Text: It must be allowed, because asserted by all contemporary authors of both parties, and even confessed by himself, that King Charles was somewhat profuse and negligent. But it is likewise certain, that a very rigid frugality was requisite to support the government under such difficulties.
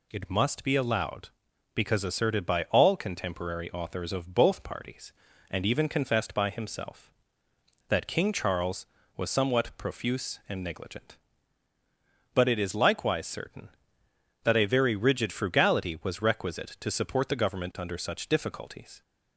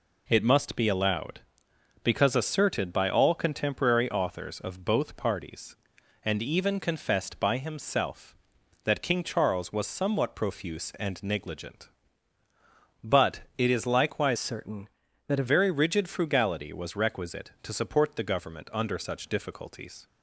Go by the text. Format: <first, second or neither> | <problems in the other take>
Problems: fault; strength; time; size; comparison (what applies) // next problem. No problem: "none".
first | changes voice from "certain" to "a"; from 14.3 to 15.4 s; 1.1 s long